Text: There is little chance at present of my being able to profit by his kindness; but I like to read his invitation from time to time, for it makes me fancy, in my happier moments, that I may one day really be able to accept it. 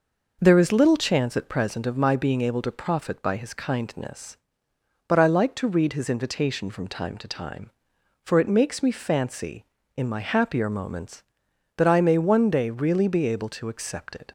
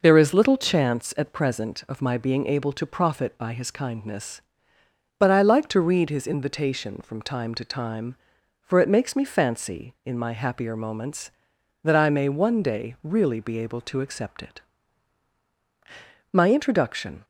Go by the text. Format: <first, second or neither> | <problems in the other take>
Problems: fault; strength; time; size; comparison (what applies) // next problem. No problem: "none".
first | goes on to say "My introduction"; noticeable; from 16.3 s on; 0.92 s long